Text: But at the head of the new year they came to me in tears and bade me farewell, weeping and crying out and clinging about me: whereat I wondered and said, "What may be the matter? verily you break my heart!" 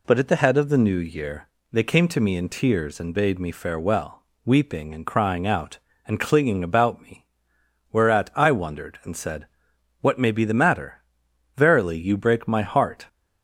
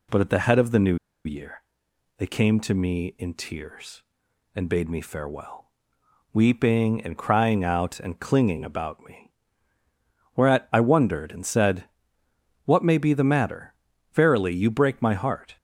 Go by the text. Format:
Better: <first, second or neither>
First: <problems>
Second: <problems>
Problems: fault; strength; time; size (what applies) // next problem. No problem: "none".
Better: first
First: pauses between "year" and "they"; slight; at 1.4 s; 0.24 s long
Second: pauses between "new" and "year"; slight; at 0.9 s; 0.29 s long // pauses between "year" and "they"; noticeable; at 1.6 s; 0.56 s long